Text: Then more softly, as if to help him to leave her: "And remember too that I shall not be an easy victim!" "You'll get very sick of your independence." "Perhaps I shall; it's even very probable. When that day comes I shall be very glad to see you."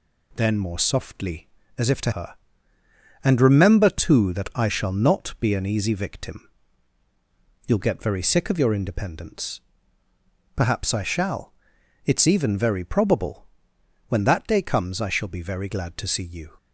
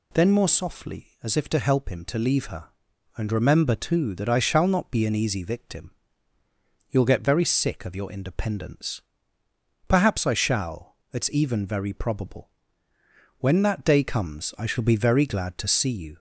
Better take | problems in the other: second | skips "help him to leave"; at 2.1 s

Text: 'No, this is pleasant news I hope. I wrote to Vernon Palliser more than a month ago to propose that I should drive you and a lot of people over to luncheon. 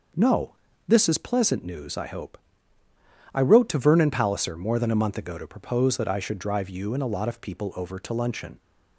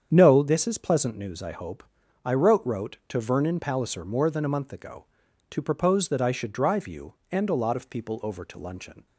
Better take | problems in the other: first | starts louder than the rest; strong; until 1.1 s; 8 dB // says "wrote" twice; at 2.6 s

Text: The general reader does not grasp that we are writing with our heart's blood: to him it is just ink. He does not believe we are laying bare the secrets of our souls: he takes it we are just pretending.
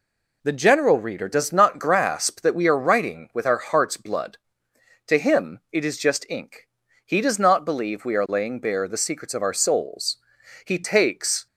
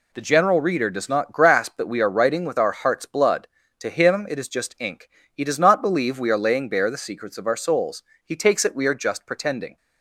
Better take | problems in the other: second | stops before "it we are just pretending"; at 11.4 s

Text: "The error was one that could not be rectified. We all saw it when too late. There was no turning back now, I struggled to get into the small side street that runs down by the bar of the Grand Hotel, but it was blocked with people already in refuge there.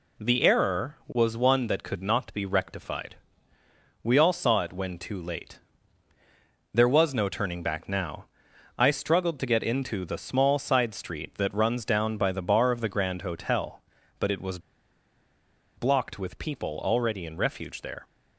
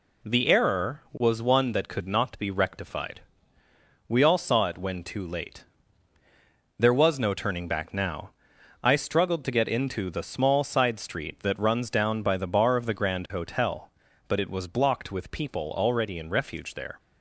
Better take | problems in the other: second | pauses between "was" and "blocked"; at 14.5 s; 1.1 s long

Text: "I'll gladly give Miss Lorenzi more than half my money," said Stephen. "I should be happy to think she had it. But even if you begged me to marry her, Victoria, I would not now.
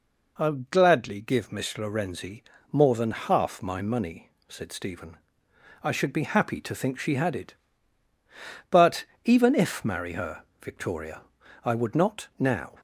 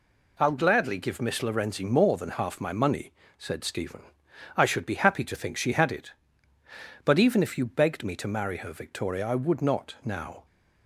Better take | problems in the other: second | pauses between "Lorenzi" and "more"; slight; at 2.4 s; 0.30 s long // pauses between "But" and "even"; slight; at 9.0 s; 0.20 s long // skips "you begged me to"; at 9.8 s

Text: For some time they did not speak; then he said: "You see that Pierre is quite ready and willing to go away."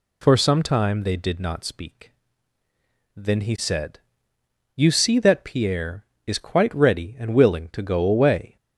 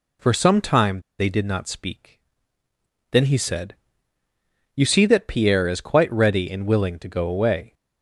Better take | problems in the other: first | pauses between "time" and "they"; slight; at 1.0 s; 0.18 s long

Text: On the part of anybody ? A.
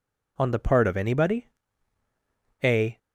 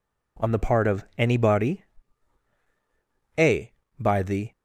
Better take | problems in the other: first | goes on to say "By the"; from 3.9 s on; 0.54 s long

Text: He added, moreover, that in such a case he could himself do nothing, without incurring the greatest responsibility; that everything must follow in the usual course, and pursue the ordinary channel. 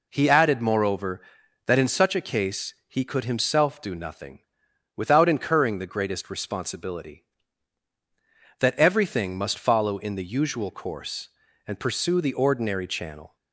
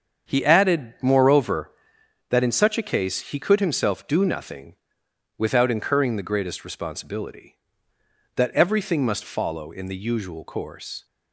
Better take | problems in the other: first | starts louder than the rest; until 1.3 s; 7 dB // stops before "and pursue the ordinary channel"; at 11.0 s

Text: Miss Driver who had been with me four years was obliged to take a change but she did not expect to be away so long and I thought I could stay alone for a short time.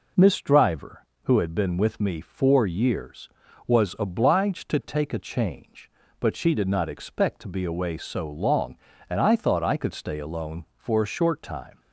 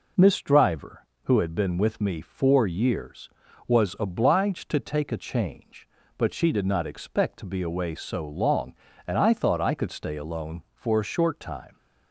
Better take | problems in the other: neither | none

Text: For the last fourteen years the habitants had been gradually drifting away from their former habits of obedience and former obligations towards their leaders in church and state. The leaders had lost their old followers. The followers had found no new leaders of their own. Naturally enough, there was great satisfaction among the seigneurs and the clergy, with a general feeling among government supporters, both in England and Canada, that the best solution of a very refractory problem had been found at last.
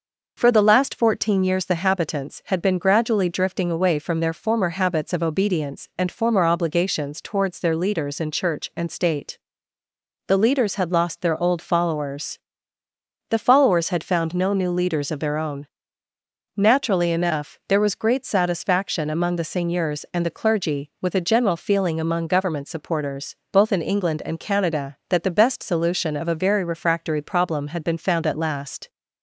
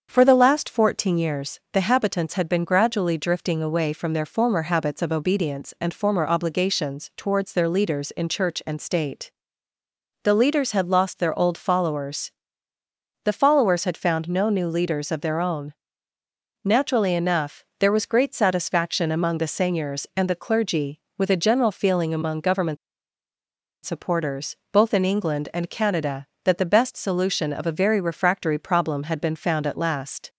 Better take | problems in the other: first | starts louder than the rest; until 1.1 s; 7 dB // pauses between "government" and "supporters"; at 22.7 s; 1.0 s long

